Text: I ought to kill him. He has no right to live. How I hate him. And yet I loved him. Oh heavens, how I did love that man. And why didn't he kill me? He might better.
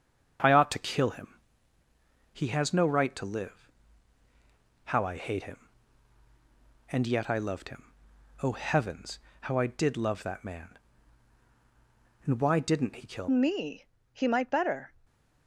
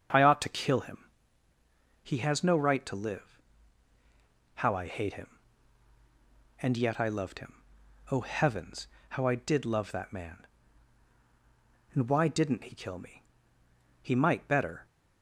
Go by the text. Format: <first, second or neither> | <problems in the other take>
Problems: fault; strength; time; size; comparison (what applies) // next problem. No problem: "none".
second | starts louder than the rest; until 2.4 s; 7 dB; also in the second // changes voice at "me"; from 13.2 s on; 1.7 s long